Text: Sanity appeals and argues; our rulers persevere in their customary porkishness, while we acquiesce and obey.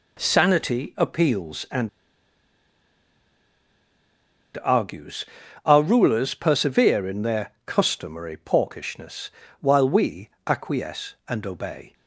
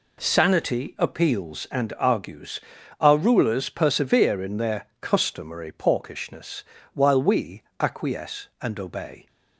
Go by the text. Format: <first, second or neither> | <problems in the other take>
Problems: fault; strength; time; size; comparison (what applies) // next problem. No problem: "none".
second | pauses between "and" and "argues"; strong; at 1.8 s; 2.6 s long // pauses between "we" and "acquiesce"; slight; at 10.2 s; 0.18 s long; slight in the second